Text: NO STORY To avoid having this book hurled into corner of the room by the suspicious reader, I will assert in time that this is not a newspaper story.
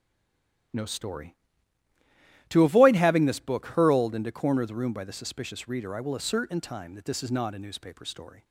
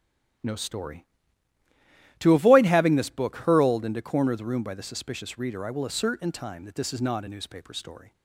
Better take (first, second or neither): second